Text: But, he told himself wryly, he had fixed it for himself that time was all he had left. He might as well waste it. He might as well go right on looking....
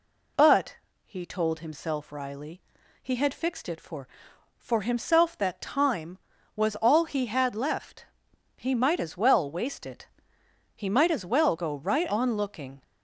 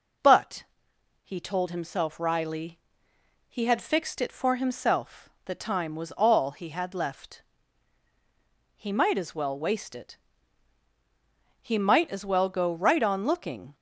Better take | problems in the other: second | says "for" twice; at 4.5 s

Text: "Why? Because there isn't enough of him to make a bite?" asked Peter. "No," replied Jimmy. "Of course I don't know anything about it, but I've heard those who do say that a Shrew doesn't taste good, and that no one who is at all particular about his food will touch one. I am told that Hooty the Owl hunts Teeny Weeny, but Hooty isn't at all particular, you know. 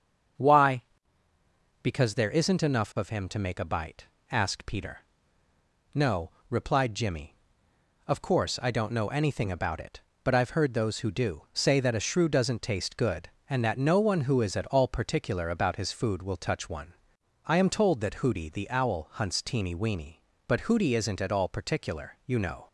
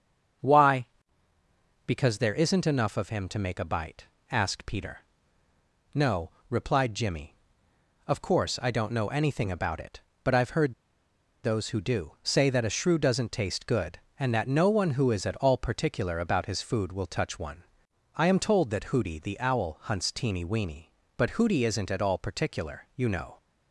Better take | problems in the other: first | starts louder than the rest; until 2.4 s; 7 dB; also in the first // pauses between "heard" and "those"; noticeable; at 10.7 s; 0.70 s long

